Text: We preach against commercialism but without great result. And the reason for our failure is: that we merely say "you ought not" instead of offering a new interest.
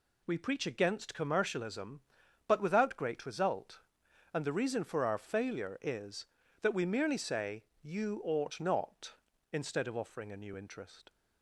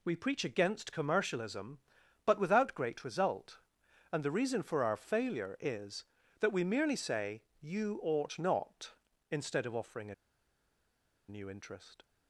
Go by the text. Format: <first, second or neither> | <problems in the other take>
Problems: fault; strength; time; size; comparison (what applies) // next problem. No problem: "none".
first | pauses between "say" and "you"; slight; at 7.4 s; 0.18 s long; slight in the first // pauses between "a" and "new"; at 10.1 s; 1.1 s long